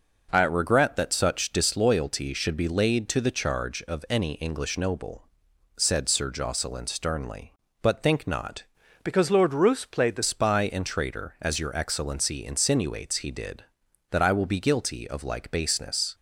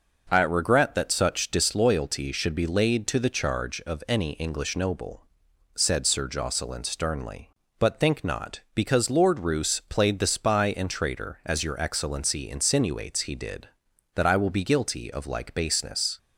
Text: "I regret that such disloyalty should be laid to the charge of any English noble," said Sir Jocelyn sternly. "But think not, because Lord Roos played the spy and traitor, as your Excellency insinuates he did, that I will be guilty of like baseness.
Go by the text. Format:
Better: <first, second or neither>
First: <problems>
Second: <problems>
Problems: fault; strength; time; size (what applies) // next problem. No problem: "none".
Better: second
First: changes voice from "because" to "the"; from 9.0 to 10.2 s; 1.2 s long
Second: none